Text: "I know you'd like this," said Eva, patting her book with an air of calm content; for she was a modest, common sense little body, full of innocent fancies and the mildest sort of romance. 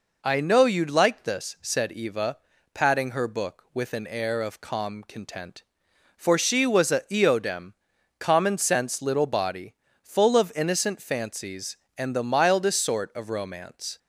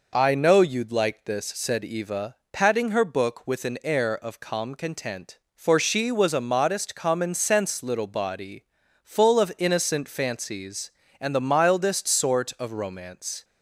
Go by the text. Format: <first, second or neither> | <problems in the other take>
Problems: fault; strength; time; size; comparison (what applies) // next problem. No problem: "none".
second | says "eodem" for "modest"; at 7.0 s